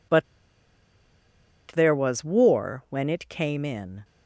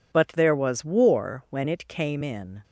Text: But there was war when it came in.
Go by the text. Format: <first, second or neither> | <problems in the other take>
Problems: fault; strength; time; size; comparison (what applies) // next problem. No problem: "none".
second | pauses between "But" and "there"; strong; at 0.2 s; 1.4 s long